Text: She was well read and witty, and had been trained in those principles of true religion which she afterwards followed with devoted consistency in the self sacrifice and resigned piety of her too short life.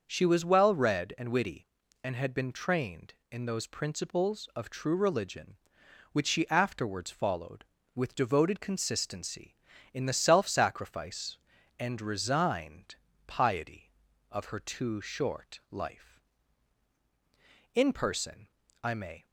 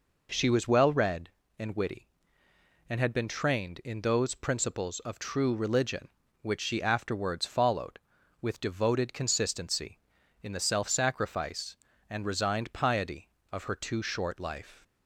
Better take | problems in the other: second | starts louder than the rest; until 1.0 s; 6.5 dB // pauses between "resigned" and "piety"; slight; at 12.9 s; 0.32 s long // goes on to say "In person I may"; from 17.7 s on; 1.5 s long

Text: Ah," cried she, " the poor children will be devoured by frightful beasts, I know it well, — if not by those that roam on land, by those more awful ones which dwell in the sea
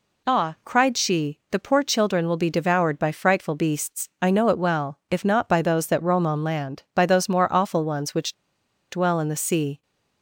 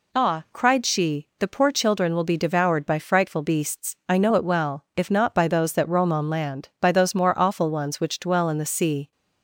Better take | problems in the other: second | pauses between "which" and "dwell"; noticeable; at 8.3 s; 0.57 s long

